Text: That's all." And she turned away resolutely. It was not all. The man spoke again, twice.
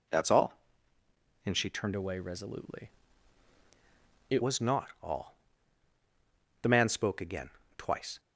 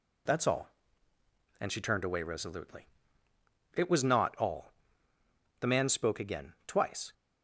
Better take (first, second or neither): second